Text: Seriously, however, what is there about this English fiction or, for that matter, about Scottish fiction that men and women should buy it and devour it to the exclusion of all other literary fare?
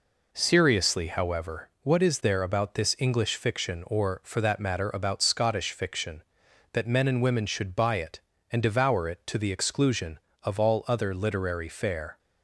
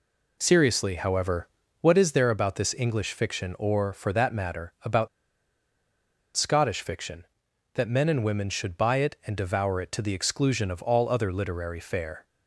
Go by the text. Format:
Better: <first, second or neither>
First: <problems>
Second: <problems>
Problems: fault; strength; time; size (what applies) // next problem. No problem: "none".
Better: first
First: none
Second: pauses between "about" and "Scottish"; strong; at 5.0 s; 1.2 s long